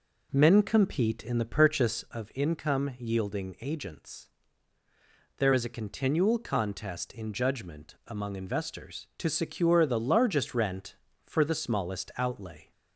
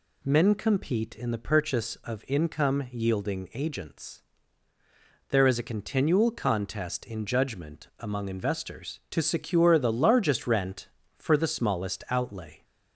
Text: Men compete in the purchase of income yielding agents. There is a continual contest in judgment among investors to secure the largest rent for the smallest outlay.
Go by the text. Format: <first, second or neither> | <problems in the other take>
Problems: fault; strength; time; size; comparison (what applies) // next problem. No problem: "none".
second | starts louder than the rest; until 2.2 s; 3.5 dB